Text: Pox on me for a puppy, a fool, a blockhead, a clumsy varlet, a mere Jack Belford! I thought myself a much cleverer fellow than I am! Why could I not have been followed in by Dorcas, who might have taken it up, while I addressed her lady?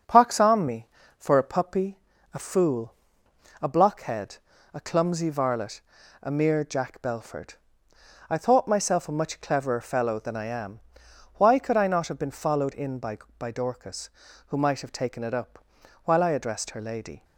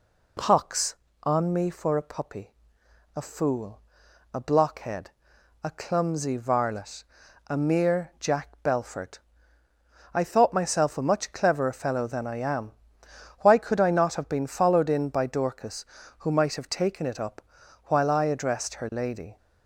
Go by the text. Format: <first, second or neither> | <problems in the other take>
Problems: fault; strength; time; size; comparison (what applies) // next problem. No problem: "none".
second | starts louder than the rest; until 1.3 s; 6.5 dB // says "by" twice; at 13.3 s